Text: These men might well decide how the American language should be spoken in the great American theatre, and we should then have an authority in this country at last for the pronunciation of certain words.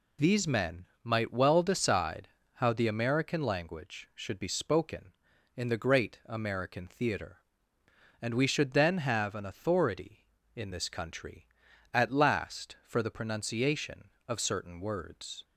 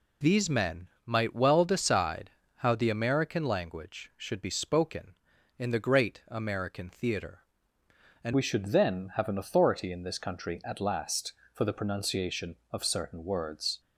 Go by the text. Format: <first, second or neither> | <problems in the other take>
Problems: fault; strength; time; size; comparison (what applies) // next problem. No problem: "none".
first | pauses between "men" and "might"; slight; at 0.8 s; 0.16 s long; slight in the first // pauses between "decide" and "how"; slight; at 2.2 s; 0.28 s long; slight in the first // changes voice at "we"; from 8.3 s on; 5.4 s long